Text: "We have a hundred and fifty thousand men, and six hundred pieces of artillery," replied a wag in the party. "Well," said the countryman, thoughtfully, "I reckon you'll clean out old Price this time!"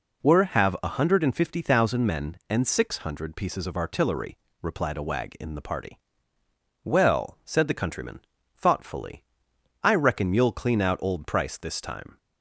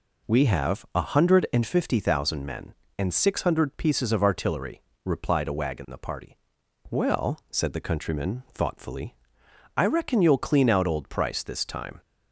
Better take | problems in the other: second | says "Were" for "We"; at 0.2 s

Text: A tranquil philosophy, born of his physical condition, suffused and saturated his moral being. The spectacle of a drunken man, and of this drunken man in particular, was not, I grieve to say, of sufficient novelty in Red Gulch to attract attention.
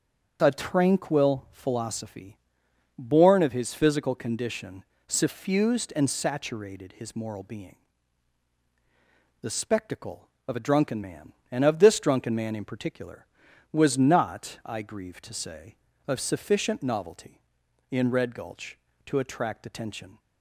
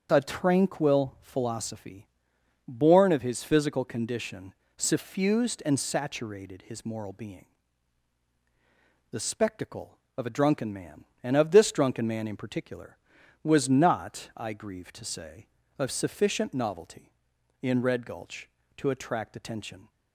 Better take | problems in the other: neither | starts louder than the rest; the same in both

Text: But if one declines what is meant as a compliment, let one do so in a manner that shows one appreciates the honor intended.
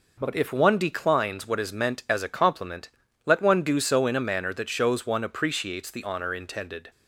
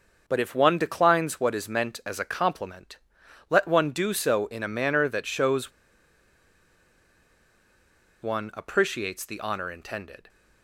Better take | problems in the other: first | starts louder than the rest; until 1.2 s; 6.5 dB // pauses between "shows" and "one"; strong; at 5.7 s; 2.5 s long

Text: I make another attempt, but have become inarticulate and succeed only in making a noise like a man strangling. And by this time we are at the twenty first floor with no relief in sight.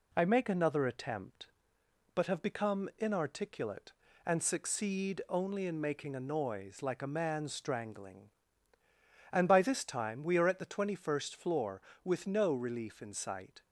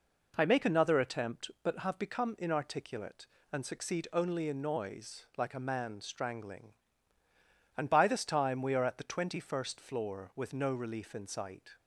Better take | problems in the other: first | skips "making a"; at 4.6 s

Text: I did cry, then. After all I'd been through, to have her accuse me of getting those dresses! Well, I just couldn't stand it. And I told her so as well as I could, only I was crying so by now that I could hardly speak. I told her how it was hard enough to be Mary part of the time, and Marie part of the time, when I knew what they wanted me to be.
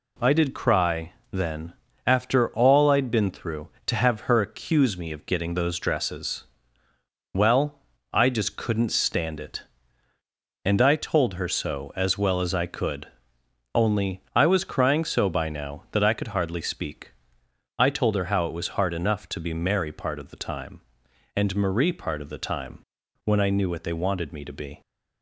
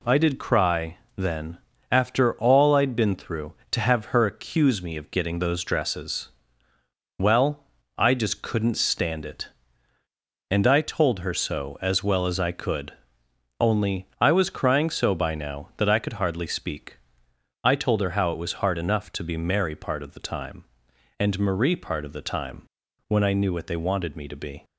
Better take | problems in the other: neither | none

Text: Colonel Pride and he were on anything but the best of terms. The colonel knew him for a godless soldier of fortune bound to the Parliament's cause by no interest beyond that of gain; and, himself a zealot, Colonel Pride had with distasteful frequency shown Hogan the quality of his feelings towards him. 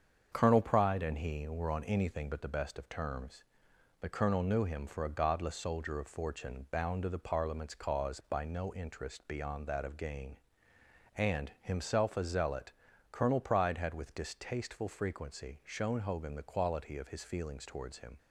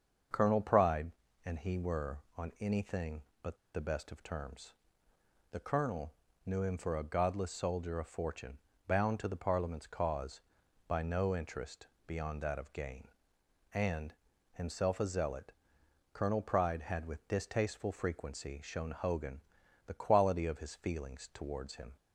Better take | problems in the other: first | starts louder than the rest; until 1.6 s; 6.5 dB; strong in the first // pauses between "but" and "the"; slight; at 3.5 s; 0.18 s long // pauses between "colonel" and "knew"; slight; at 6.1 s; 0.32 s long // pauses between "fortune" and "bound"; slight; at 8.5 s; 0.30 s long // pauses between "interest" and "beyond"; slight; at 11.8 s; 0.22 s long // pauses between "Hogan" and "the"; at 19.4 s; 0.44 s long

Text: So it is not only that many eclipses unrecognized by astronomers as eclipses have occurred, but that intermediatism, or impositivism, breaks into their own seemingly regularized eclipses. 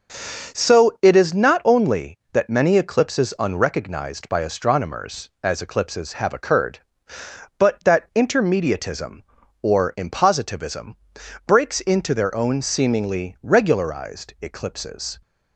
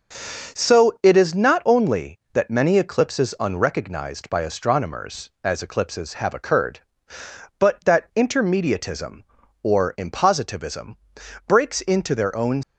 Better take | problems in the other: first | starts louder than the rest; until 1.6 s; 6.5 dB; also in the first // stops before "seemingly regularized eclipses"; at 12.6 s

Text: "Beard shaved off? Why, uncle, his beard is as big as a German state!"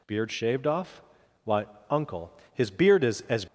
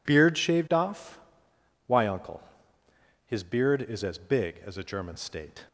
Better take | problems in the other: second | stops before "big as a German state"; at 3.4 s

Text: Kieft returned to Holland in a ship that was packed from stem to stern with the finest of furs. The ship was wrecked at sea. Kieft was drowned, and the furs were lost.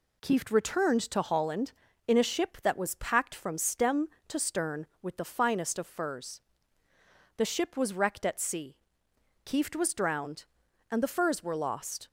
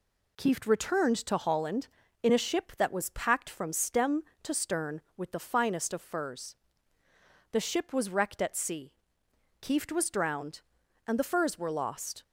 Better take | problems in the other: neither | none

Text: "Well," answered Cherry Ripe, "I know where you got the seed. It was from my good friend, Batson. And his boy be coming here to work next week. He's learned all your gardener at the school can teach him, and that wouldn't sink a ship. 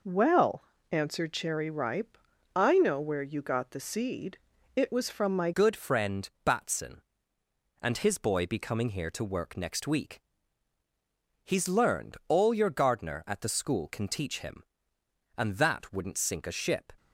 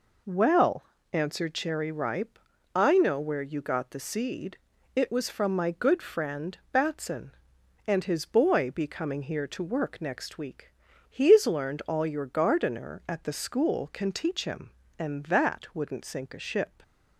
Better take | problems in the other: second | changes voice at "good"; from 5.5 s on; 11.4 s long

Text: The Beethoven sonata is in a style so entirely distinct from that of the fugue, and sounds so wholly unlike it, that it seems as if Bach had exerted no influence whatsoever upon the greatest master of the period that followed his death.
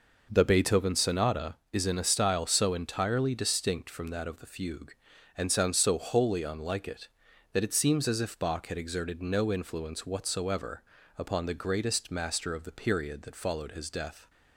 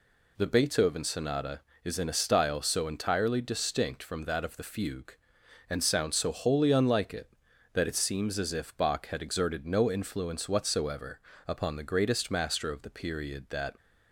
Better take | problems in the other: first | pauses between "whatsoever" and "upon"; slight; at 11.2 s; 0.26 s long; slight in the first // stops before "followed his death"; at 13.7 s

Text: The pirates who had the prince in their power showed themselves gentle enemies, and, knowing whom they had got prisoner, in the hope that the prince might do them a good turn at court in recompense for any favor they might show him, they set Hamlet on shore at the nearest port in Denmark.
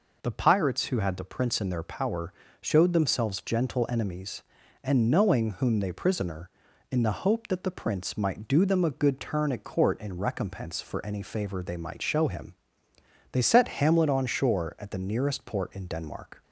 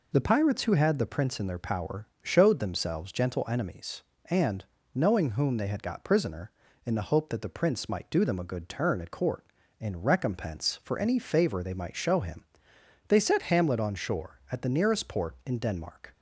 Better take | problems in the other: second | pauses between "power" and "showed"; slight; at 2.3 s; 0.28 s long; slight in the second // skips "had got"; at 5.9 s

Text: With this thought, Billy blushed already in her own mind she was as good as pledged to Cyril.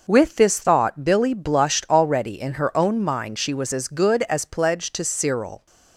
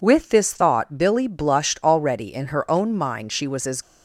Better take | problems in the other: first | stops before "good as pledged to Cyril"; at 3.8 s

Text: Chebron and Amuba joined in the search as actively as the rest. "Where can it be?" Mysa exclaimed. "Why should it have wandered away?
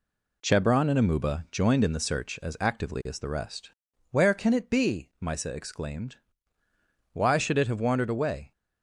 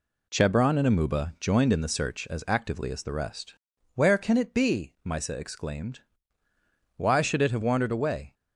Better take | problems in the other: neither | none

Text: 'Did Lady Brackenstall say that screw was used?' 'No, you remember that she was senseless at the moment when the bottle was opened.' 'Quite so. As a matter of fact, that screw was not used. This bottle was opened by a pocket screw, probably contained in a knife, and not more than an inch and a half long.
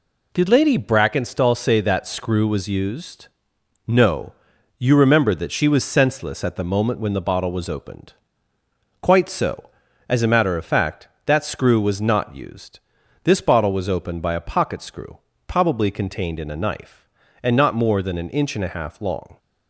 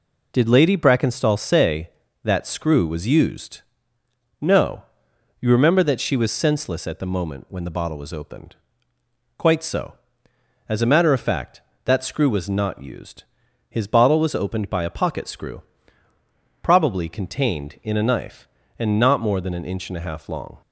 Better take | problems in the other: first | says "His" for "This"; at 13.6 s

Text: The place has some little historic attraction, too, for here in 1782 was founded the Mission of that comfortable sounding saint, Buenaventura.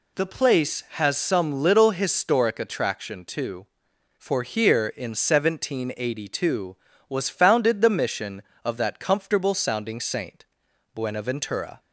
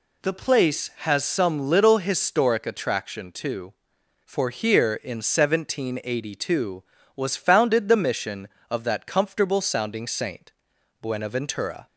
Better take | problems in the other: neither | none

